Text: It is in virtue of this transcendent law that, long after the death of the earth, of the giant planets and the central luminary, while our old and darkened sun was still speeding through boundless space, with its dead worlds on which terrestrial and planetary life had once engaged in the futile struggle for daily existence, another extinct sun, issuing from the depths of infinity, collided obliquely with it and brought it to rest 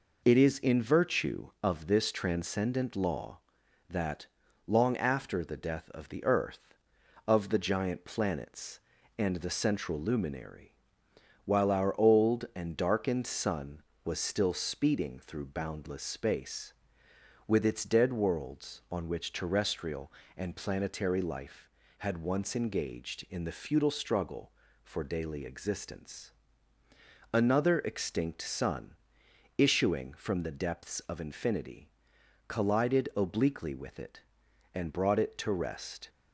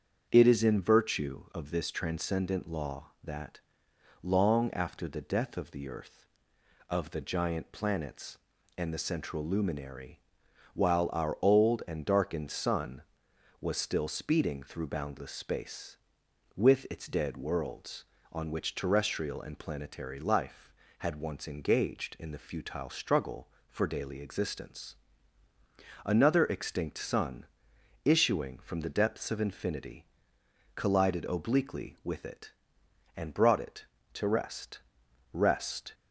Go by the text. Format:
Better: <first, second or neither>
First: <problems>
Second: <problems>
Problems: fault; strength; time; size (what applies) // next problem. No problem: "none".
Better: first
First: none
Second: starts louder than the rest; strong; until 1.3 s; 7.5 dB // says "rest" twice; at 35.3 s